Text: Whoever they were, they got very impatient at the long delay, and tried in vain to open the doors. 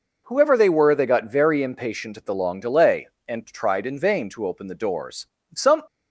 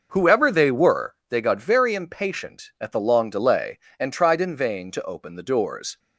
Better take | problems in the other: second | goes on to say "Some"; slight; from 5.5 s on; 0.28 s long

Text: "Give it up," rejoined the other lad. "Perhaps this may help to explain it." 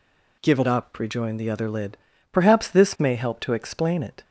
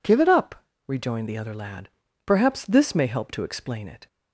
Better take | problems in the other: second | says "lid" for "lad"; at 1.6 s

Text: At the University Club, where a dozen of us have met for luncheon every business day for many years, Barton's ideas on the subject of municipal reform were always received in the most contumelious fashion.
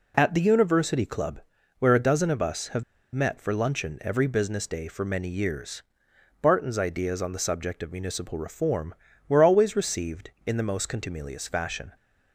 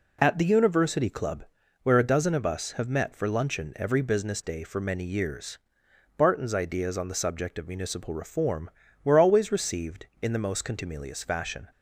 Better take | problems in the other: second | pauses between "have" and "met"; slight; at 2.8 s; 0.31 s long

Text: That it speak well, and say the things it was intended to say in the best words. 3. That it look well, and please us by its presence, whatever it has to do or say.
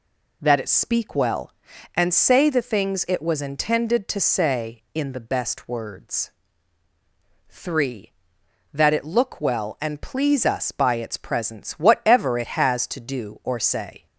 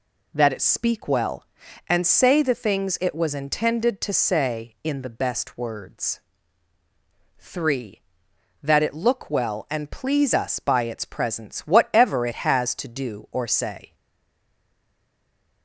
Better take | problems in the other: first | stays silent after the last word; noticeable; from 13.9 s on; 1.7 s long

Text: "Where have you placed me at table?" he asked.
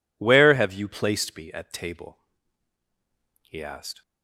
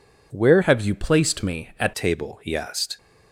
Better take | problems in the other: first | changes voice from "have" to "at"; from 0.6 to 1.9 s; 1.3 s long

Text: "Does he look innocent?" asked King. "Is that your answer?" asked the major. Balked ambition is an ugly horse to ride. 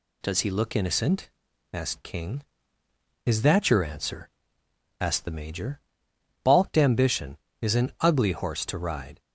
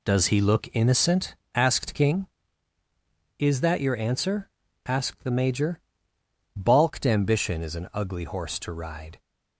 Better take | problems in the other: neither | none

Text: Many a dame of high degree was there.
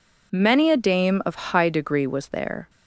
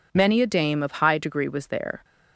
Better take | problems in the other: neither | none

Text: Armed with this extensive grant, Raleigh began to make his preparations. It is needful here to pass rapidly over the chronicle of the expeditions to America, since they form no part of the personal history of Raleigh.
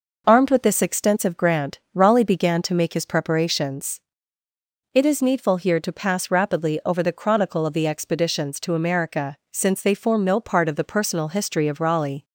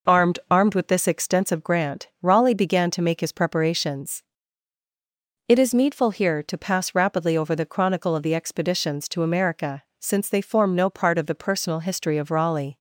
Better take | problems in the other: first | says "Armed" twice; at 0.4 s

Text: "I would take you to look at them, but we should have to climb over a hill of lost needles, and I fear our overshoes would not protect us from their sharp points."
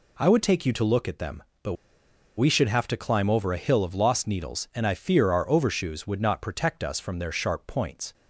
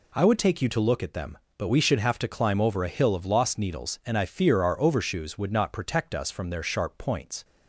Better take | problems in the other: second | pauses between "but" and "we"; noticeable; at 1.7 s; 0.62 s long

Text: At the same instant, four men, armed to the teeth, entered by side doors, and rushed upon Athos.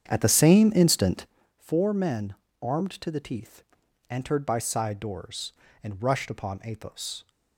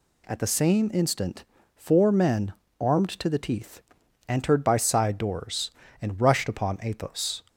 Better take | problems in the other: second | starts louder than the rest; strong; until 1.4 s; 8.5 dB

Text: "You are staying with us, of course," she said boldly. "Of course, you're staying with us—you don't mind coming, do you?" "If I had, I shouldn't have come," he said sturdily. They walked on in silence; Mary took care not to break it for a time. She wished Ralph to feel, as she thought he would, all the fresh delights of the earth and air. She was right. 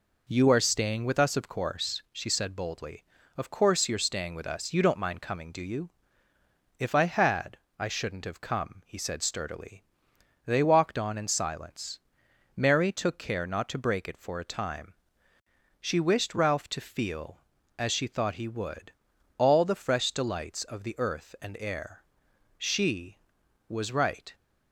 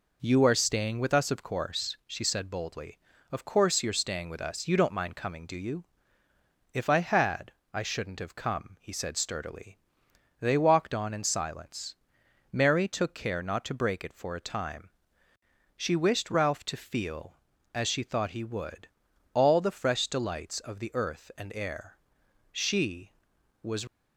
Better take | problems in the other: first | stops before "right"; at 23.8 s

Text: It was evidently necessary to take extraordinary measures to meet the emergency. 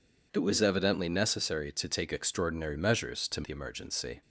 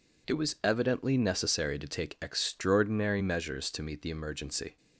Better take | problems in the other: second | skips "meet"; at 3.4 s

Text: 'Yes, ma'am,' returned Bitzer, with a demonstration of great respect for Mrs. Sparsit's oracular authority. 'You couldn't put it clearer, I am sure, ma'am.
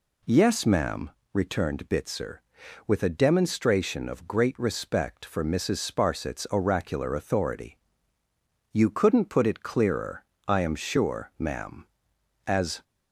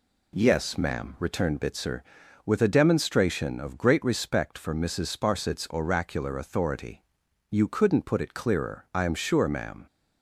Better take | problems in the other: second | goes on to say "As"; slight; from 12.4 s on; 0.36 s long

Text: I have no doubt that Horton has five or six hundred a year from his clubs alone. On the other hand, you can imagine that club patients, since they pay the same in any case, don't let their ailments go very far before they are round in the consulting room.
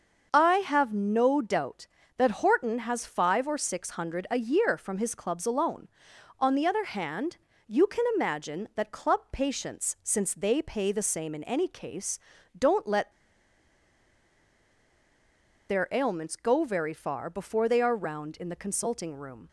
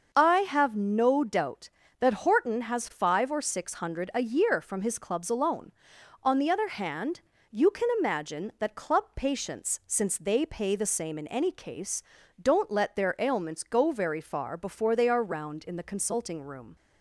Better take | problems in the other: second | starts louder than the rest; until 1.3 s; 6.5 dB; also in the second // pauses between "let" and "their"; strong; at 13.1 s; 2.5 s long

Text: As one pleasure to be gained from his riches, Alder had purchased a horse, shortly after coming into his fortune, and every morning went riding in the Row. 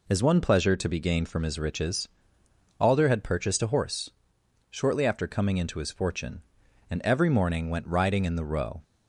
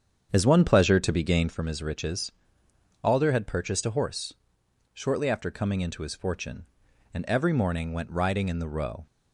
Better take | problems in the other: first | starts louder than the rest; strong; until 1.5 s; 8 dB

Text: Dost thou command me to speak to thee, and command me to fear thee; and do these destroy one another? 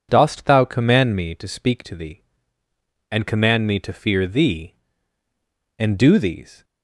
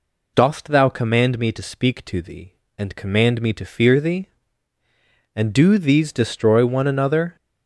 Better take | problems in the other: second | stops before "destroy one another"; at 6.6 s

